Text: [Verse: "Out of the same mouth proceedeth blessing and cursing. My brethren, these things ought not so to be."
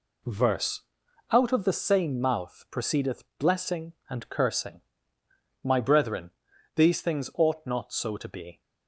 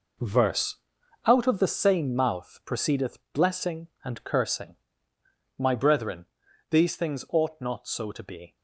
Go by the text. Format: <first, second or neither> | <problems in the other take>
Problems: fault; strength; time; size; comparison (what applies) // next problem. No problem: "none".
first | gets quieter; strong; throughout; 10 dB // pauses between "proceedeth" and "blessing"; slight; at 3.1 s; 0.16 s long; slight in the first